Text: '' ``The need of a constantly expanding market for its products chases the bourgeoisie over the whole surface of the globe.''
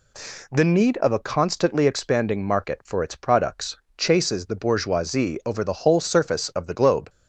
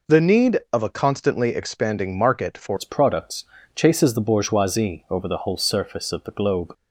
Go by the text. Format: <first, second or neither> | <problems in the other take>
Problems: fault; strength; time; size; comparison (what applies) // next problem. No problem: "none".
first | changes voice at "its"; from 2.7 s on; 4.0 s long // pauses between "products" and "chases"; slight; at 3.4 s; 0.32 s long; slight in the first